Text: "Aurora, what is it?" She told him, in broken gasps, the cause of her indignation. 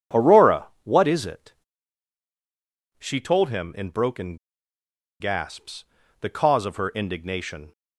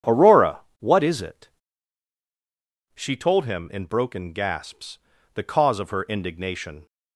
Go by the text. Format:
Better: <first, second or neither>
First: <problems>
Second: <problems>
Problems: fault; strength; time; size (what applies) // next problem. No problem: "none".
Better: second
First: pauses between "broken" and "gasps"; noticeable; at 4.3 s; 0.84 s long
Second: none